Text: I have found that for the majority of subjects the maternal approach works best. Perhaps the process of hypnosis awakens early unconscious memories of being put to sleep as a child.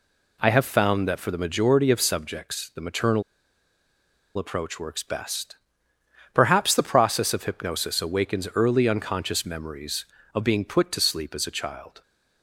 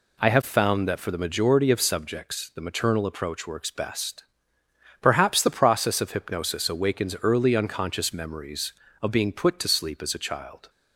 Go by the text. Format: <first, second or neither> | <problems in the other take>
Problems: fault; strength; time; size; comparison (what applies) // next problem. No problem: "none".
second | pauses between "maternal" and "approach"; at 3.2 s; 1.1 s long